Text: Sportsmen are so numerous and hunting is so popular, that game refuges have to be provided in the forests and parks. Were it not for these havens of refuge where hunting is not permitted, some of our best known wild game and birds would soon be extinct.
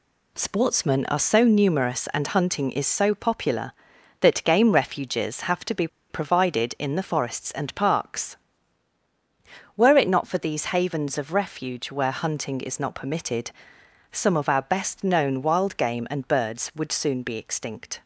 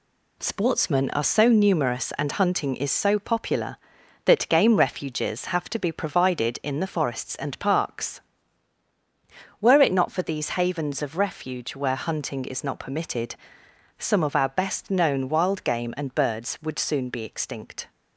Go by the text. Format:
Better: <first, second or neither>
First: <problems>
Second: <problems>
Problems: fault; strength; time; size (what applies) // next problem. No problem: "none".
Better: second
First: pauses between "be" and "provided"; slight; at 5.8 s; 0.23 s long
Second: none